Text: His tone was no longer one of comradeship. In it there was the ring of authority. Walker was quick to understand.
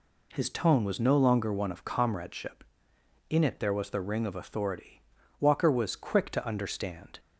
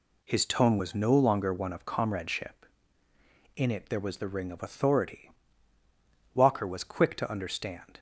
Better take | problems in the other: neither | none

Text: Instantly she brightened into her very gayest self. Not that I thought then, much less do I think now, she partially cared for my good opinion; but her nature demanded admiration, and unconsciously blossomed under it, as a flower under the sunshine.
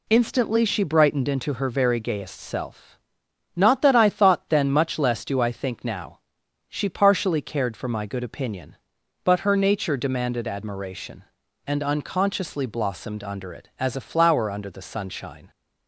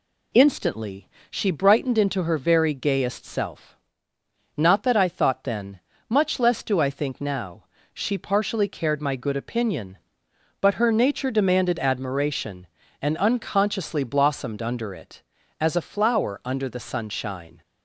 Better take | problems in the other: first | pauses between "Instantly" and "she"; slight; at 1.0 s; 0.22 s long // skips "for"; at 9.0 s

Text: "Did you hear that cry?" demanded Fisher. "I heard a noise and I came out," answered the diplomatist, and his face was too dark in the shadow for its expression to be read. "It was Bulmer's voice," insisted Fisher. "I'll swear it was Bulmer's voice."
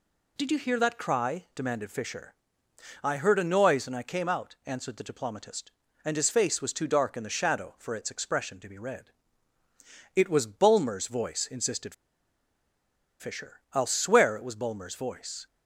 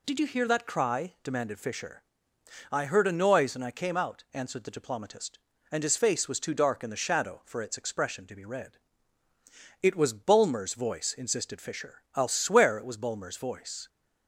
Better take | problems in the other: second | pauses between "insisted" and "Fisher"; strong; at 11.9 s; 1.2 s long

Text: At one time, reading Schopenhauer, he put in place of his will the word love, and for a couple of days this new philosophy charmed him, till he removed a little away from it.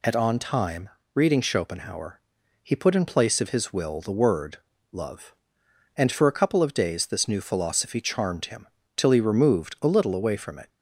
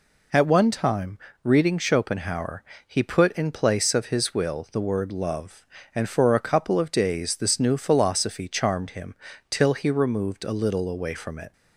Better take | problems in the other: second | says "on" for "one"; at 0.1 s // pauses between "word" and "love"; slight; at 4.5 s; 0.34 s long

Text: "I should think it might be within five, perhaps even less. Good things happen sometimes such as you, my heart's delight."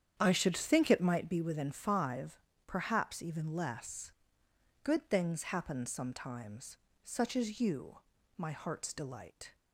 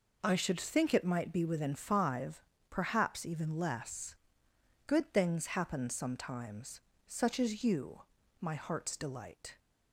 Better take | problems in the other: second | starts louder than the rest; strong; until 1.4 s; 9 dB // pauses between "sometimes" and "such"; slight; at 6.7 s; 0.26 s long; slight in the second

